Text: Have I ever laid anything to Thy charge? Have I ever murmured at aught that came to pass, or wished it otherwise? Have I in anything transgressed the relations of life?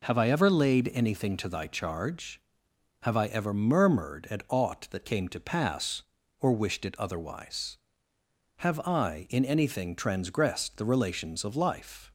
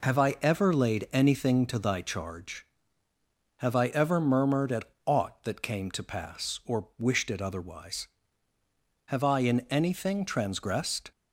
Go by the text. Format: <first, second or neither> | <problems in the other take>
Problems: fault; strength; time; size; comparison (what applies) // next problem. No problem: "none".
first | pauses between "at" and "aught"; slight; at 4.8 s; 0.16 s long // stops before "the relations of life"; at 11.1 s